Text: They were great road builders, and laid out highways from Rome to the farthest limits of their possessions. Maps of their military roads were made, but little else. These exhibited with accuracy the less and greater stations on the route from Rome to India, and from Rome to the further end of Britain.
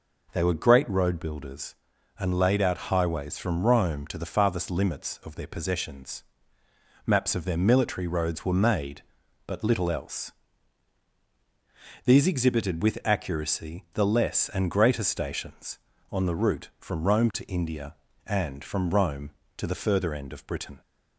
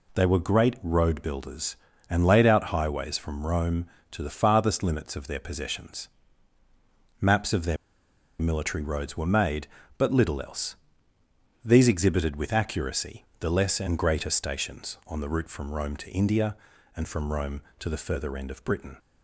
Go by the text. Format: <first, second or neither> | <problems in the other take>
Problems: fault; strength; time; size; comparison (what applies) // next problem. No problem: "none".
first | pauses between "their" and "military"; noticeable; at 7.7 s; 0.63 s long // pauses between "accuracy" and "the"; slight; at 13.2 s; 0.16 s long